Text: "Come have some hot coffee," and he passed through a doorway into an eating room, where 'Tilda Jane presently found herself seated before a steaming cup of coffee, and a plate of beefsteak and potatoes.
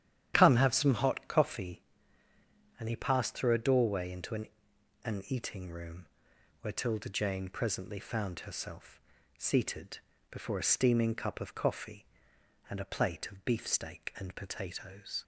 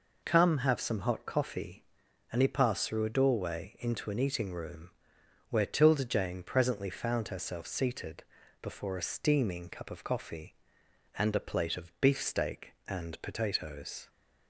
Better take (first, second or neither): second